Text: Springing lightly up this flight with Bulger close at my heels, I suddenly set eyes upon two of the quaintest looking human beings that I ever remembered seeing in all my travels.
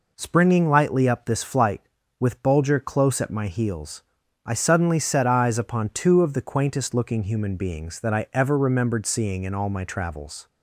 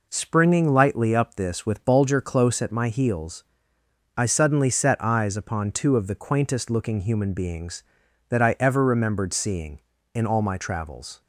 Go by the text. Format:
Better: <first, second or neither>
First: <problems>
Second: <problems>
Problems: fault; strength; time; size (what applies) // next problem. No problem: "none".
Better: first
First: none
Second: skips "flight"; at 1.6 s